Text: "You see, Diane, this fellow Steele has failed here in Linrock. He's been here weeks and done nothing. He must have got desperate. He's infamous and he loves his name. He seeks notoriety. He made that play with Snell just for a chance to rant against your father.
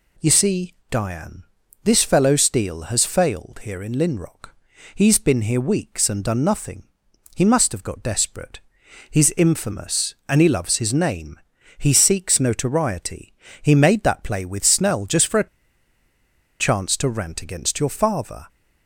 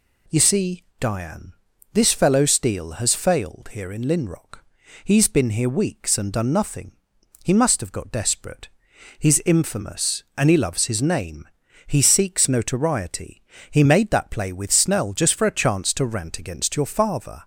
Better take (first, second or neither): second